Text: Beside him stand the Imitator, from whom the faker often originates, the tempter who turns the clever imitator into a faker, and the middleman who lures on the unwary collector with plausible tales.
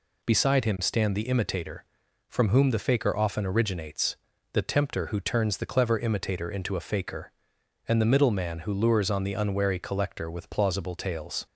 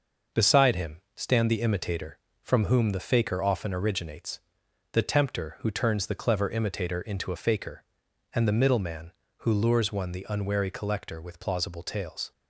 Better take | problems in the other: first | says "one" for "on"; at 9.9 s

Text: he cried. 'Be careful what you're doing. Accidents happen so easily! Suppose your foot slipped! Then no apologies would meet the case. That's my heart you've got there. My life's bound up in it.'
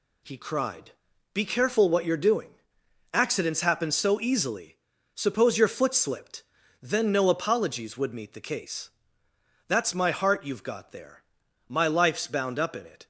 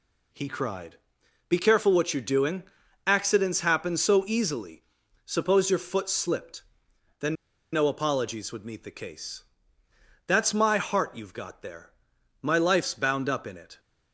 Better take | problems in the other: first | pauses between "Then" and "no"; at 7.3 s; 0.38 s long

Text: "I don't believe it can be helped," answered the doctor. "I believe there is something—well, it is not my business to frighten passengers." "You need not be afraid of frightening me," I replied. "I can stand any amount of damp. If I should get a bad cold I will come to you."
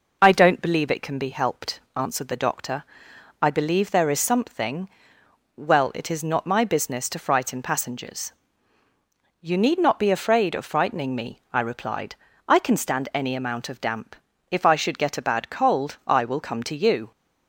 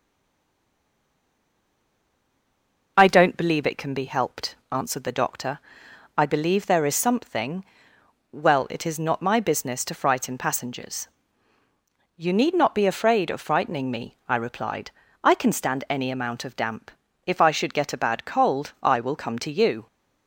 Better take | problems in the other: first | stays silent before the first word; strong; until 2.9 s; 2.9 s long

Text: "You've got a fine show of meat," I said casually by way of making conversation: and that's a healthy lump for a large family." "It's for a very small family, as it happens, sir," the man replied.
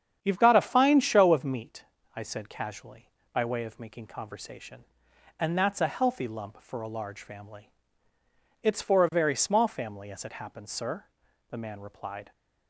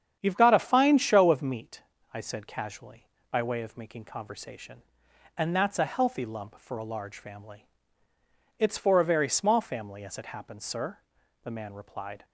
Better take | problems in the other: neither | starts louder than the rest; strong; the same in both

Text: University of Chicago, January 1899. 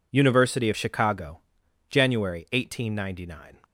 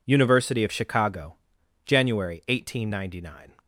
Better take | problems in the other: neither | none

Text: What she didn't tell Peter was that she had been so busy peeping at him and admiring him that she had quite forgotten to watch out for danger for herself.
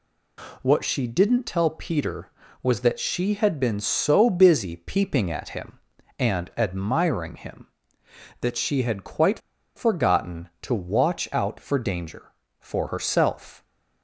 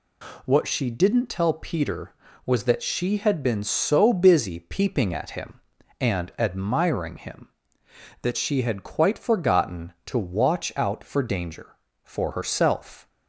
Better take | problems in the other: second | pauses between "quite" and "forgotten"; at 9.3 s; 0.37 s long

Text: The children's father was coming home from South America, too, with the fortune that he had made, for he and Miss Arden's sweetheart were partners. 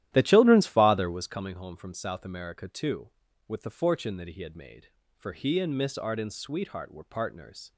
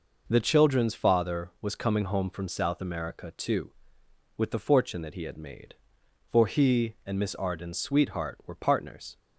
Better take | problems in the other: second | starts louder than the rest; strong; until 1.4 s; 13 dB

